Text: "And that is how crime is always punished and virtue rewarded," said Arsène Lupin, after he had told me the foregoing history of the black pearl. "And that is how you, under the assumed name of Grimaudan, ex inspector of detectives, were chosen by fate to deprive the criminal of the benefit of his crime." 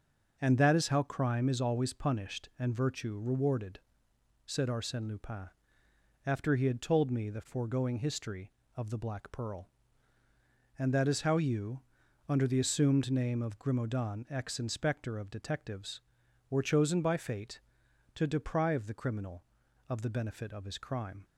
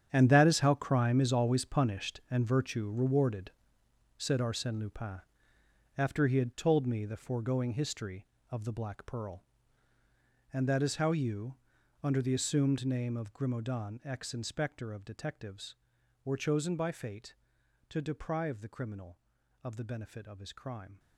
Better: first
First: starts louder than the rest; noticeable; until 1.4 s; 6 dB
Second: gets quieter; strong; throughout; 13.5 dB // starts louder than the rest; strong; until 1.1 s; 9 dB

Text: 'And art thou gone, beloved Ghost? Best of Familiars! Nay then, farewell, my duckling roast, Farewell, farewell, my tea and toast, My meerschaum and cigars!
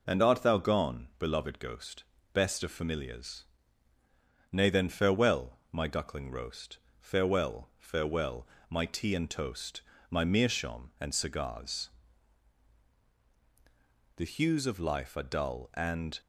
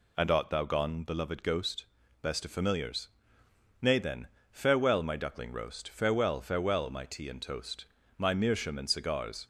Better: second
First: goes on to say "The hues of life are dull and"; strong; from 14.1 s on; 2.0 s long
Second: none

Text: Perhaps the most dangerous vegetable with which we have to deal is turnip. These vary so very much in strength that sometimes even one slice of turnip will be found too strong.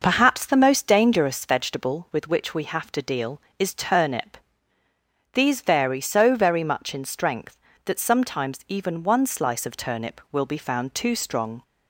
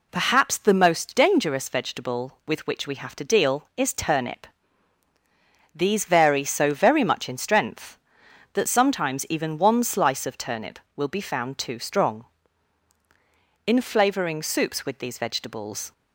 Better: first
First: none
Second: goes on to say "In flavouring soups with these vegetables"; strong; from 13.6 s on; 2.2 s long

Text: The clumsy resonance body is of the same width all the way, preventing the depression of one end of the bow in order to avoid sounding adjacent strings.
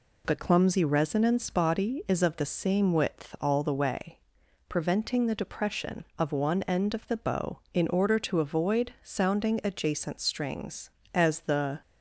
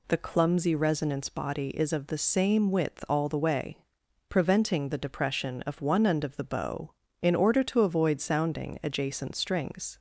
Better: second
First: goes on to say "As the"; noticeable; from 11.1 s on; 0.66 s long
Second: none

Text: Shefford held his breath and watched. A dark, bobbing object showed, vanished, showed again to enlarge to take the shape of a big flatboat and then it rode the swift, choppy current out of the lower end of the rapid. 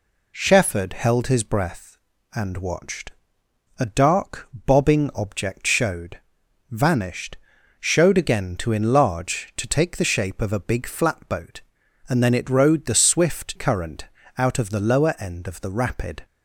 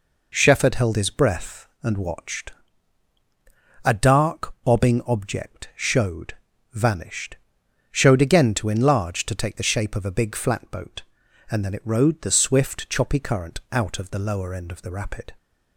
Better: second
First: skips "choppy"; at 13.5 s // pauses between "current" and "out"; slight; at 14.0 s; 0.32 s long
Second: none

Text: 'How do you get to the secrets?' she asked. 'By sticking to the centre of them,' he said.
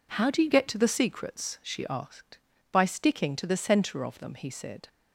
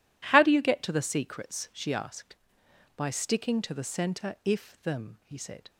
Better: first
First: none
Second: says "if" for "of"; at 4.4 s

